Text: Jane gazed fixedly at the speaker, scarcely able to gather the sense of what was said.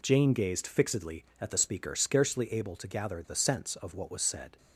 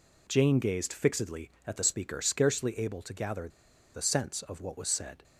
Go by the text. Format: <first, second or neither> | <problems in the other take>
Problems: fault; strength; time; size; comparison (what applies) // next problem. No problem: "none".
first | pauses between "gather" and "the"; at 3.4 s; 0.44 s long